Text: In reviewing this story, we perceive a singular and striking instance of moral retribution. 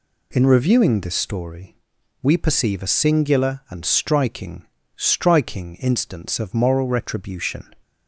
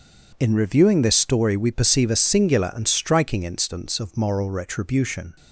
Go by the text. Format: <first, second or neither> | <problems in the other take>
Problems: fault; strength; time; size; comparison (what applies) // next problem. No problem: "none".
second | says "striking" twice; at 4.9 s